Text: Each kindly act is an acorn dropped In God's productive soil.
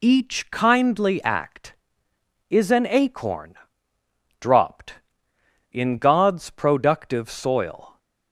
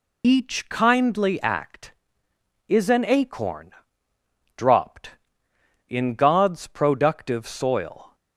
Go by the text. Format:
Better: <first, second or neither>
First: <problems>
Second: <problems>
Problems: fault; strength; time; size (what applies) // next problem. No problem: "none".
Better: first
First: pauses between "acorn" and "dropped"; noticeable; at 3.5 s; 0.86 s long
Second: loses the start of "Each"; at 0.2 s; 30 ms // pauses between "acorn" and "dropped"; noticeable; at 3.7 s; 0.86 s long